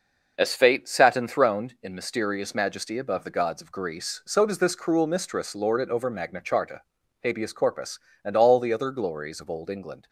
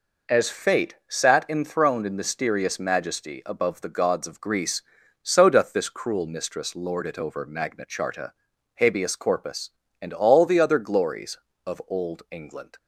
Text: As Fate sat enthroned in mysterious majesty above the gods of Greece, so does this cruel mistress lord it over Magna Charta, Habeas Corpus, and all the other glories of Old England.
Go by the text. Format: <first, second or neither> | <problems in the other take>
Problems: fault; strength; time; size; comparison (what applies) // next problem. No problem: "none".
first | says "doth" for "does"; at 5.4 s